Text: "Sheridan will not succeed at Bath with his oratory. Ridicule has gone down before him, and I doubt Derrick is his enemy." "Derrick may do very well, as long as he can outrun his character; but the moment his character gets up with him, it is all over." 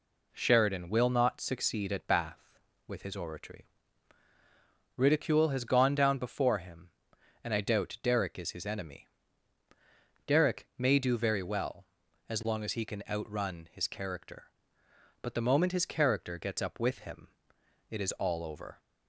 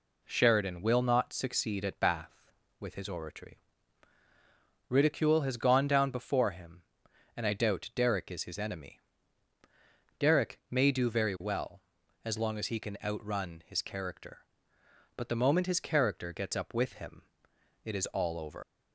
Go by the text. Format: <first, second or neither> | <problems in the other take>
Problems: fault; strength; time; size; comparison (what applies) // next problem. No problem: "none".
first | leaves "over" unfinished; at 18.6 s; 105 ms